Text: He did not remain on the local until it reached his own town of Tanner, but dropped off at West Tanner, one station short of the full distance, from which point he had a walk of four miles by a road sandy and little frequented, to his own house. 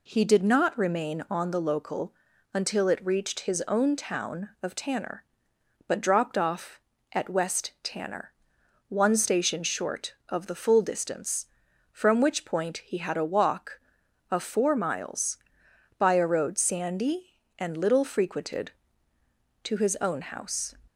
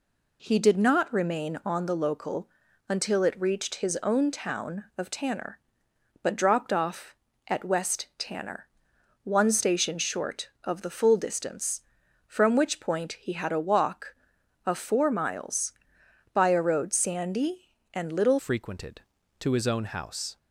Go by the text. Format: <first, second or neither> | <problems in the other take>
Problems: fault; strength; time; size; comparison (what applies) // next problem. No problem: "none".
first | pauses between "local" and "until"; at 2.4 s; 0.40 s long; also in the first // changes voice at "frequented"; from 18.3 s on; 2.0 s long